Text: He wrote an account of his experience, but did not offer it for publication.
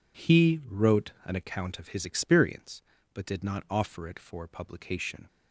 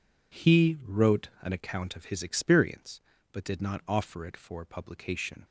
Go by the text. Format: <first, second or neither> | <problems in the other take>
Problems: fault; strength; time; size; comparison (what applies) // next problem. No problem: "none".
neither | none